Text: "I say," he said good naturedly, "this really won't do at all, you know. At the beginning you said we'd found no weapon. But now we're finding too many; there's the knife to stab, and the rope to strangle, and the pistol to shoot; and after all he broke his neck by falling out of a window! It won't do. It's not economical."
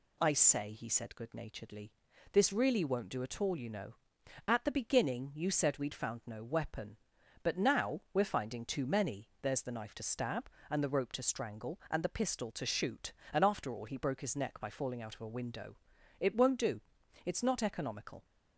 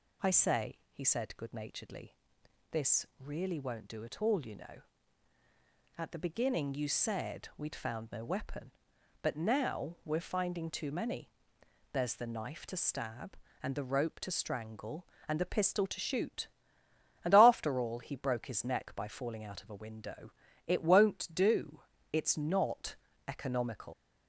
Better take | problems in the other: first | pauses between "not" and "economical"; slight; at 22.9 s; 0.32 s long // leaves "economical" unfinished; at 23.9 s; 100 ms

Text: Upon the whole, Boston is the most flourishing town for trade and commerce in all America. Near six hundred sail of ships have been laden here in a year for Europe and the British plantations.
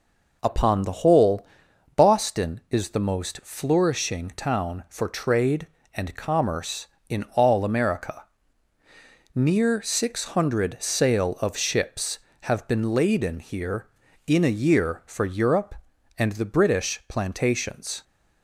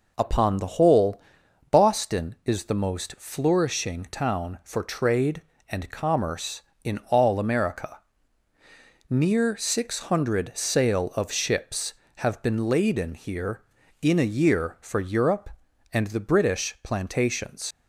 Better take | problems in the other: first | leaves "plantations" unfinished; at 17.7 s; 70 ms

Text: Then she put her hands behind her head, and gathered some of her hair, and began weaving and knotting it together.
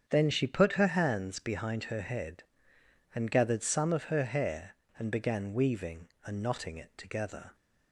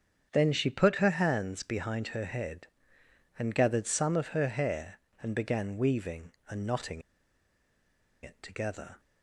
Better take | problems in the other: first | starts louder than the rest; strong; until 1.3 s; 8 dB; strong in the first // pauses between "knotting" and "it"; at 7.0 s; 1.2 s long

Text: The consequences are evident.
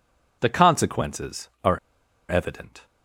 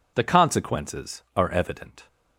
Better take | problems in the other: second | pauses between "are" and "evident"; noticeable; at 1.7 s; 0.49 s long

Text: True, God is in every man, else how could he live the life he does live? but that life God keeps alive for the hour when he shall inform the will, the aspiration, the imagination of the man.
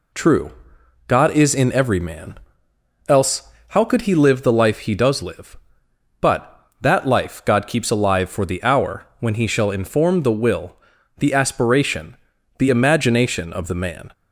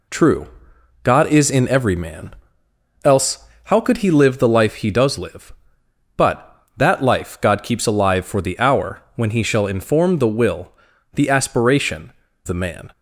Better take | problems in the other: first | pauses between "else" and "how"; slight; at 3.4 s; 0.20 s long; slight in the first // skips "the imagination of"; at 12.2 s

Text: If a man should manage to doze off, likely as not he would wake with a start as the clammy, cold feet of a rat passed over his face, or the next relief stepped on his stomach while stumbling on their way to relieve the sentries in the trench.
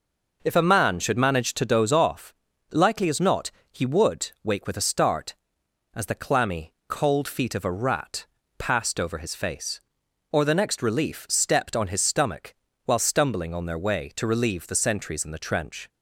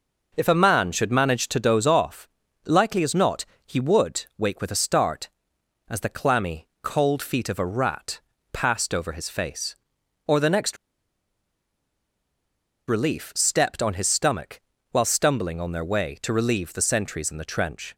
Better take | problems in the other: first | pauses between "not" and "he"; slight; at 3.4 s; 0.22 s long; slight in the first // pauses between "rat" and "passed"; slight; at 8.2 s; 0.32 s long; slight in the first // pauses between "next" and "relief"; strong; at 10.7 s; 2.1 s long // pauses between "stomach" and "while"; slight; at 14.6 s; 0.30 s long; slight in the first

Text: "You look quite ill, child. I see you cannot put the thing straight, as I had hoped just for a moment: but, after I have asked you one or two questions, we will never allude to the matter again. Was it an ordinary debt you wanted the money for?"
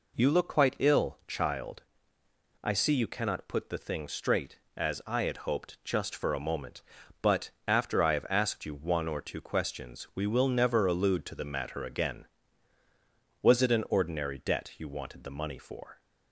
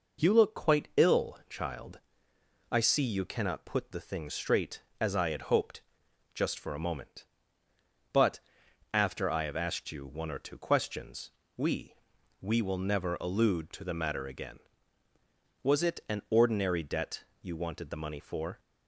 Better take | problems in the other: first | pauses between "hoped" and "just"; noticeable; at 5.7 s; 0.54 s long // says "we" twice; at 12.4 s // pauses between "debt" and "you"; slight; at 17.2 s; 0.18 s long

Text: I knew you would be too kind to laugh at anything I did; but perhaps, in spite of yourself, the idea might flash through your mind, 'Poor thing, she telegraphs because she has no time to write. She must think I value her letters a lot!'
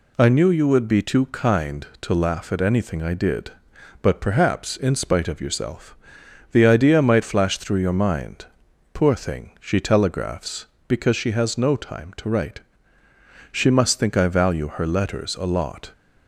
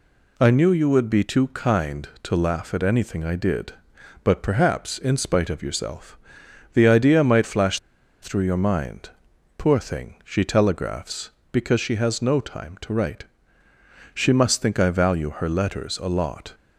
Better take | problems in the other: first | pauses between "flash" and "through"; at 7.7 s; 0.42 s long

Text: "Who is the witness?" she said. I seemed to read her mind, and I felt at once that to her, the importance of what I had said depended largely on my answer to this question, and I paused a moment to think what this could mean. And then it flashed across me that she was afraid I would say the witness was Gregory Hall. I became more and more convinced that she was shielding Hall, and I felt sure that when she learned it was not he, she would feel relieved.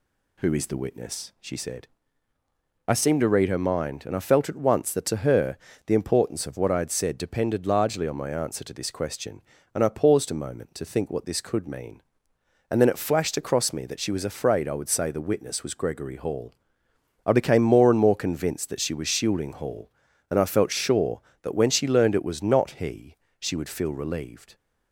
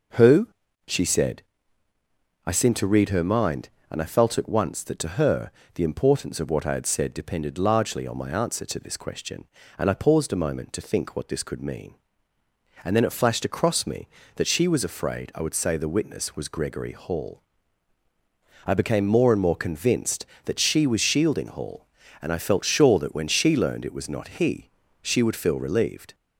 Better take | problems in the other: first | skips "is the witness"; at 0.6 s

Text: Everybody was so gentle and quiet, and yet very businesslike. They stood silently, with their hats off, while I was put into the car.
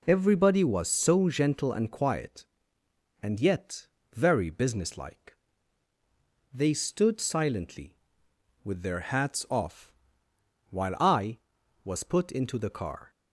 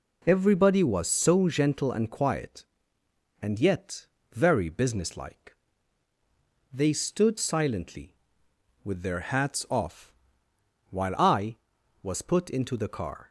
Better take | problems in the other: neither | pauses between "yet" and "very"; slight; the same in both

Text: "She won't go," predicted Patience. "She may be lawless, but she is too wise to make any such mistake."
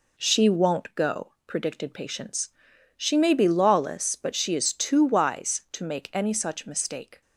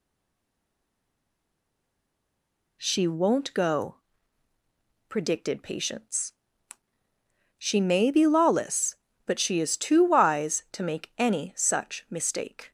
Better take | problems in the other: first | stays silent before the first word; strong; until 2.8 s; 2.8 s long

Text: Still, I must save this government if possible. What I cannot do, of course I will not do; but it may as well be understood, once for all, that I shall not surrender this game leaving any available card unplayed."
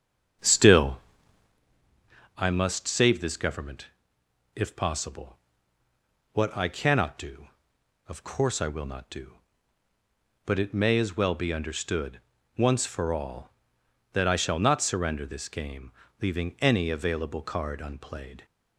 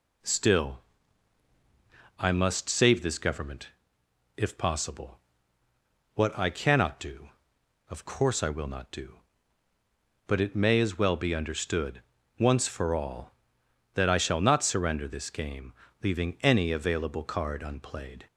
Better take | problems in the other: second | starts louder than the rest; strong; until 1.6 s; 8 dB // pauses between "government" and "if"; noticeable; at 3.8 s; 0.68 s long; noticeable in the second // pauses between "game" and "leaving"; slight; at 15.9 s; 0.30 s long; slight in the second

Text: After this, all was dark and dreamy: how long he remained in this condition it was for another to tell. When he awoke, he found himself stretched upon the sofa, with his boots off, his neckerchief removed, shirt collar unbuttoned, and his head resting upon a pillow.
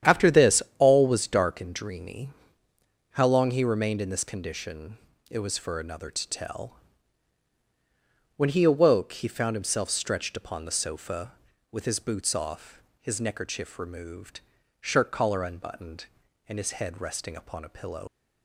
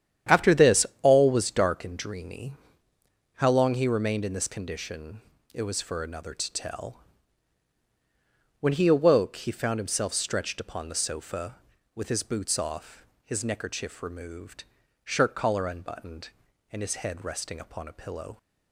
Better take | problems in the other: second | starts louder than the rest; strong; until 1.2 s; 10 dB; strong in the second // pauses between "condition" and "it"; slight; at 4.9 s; 0.32 s long; slight in the second // leaves "pillow" unfinished; at 18.0 s; 65 ms

